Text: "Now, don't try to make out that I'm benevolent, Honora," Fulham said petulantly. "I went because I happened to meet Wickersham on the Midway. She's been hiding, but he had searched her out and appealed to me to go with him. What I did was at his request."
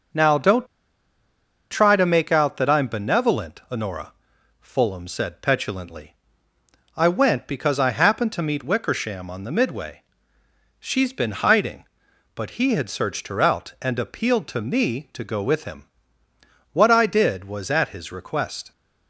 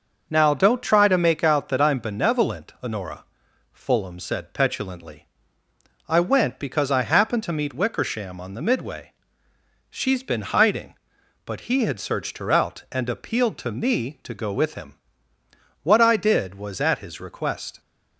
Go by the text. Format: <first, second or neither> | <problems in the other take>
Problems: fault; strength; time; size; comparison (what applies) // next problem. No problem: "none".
second | starts louder than the rest; noticeable; until 2.1 s; 6 dB; noticeable in the second // pauses between "don't" and "try"; at 0.6 s; 1.0 s long